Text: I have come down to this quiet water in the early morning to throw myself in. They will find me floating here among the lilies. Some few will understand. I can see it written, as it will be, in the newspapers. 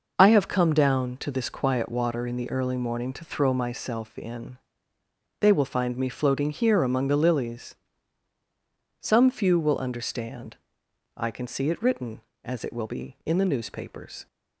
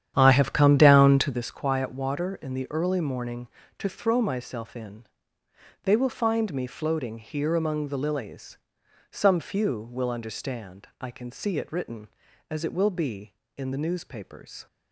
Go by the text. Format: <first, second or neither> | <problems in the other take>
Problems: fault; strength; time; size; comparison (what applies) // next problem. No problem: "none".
first | starts louder than the rest; strong; until 1.5 s; 10 dB